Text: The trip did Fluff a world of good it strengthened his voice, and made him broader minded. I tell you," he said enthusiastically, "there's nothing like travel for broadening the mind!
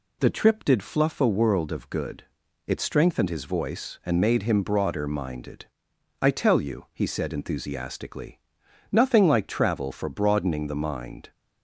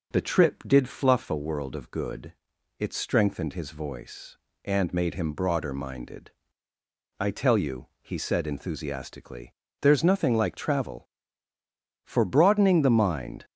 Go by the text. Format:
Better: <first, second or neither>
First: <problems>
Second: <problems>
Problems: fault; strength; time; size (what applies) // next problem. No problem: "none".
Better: second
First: pauses between "good" and "it"; at 2.2 s; 0.42 s long // skips "there's"; at 8.6 s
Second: pauses between "good" and "it"; noticeable; at 2.3 s; 0.48 s long